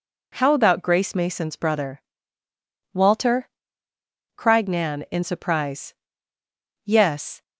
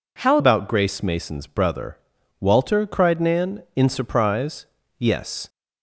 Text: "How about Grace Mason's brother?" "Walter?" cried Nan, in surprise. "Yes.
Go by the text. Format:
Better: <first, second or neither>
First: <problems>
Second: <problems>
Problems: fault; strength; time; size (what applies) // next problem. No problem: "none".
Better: first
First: none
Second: changes voice at "about"; from 0.3 s on; 5.1 s long